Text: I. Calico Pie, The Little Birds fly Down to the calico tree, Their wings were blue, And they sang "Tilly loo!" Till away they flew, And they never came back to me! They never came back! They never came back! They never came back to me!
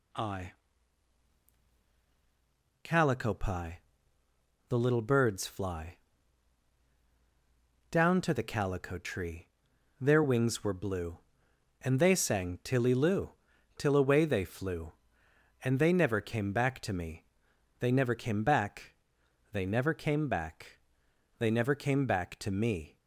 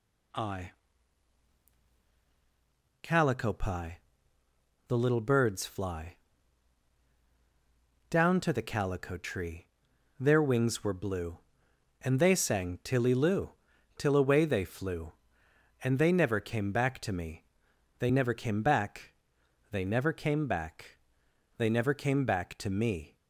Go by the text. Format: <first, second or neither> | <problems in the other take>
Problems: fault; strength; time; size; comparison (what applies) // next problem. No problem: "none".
neither | pauses between "fly" and "Down"; strong; the same in both